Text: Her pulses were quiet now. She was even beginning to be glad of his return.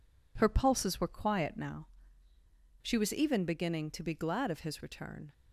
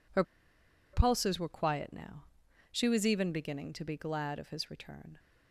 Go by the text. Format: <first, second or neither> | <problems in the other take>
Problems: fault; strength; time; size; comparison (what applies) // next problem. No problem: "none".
first | pauses between "Her" and "pulses"; noticeable; at 0.2 s; 0.69 s long